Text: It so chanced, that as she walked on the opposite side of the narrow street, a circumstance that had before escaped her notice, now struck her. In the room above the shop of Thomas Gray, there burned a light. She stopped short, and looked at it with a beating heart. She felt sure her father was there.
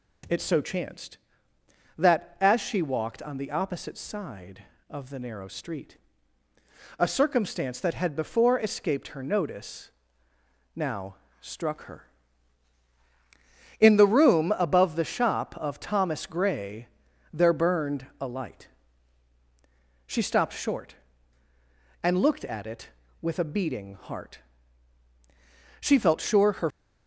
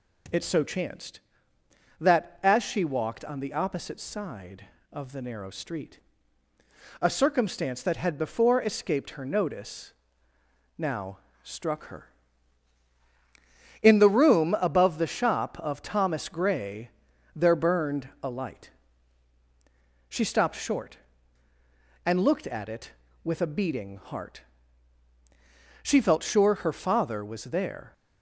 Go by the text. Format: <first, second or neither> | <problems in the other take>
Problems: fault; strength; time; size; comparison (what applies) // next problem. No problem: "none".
second | pauses between "now" and "struck"; slight; at 11.1 s; 0.24 s long; slight in the second // stops before "father was there"; at 26.7 s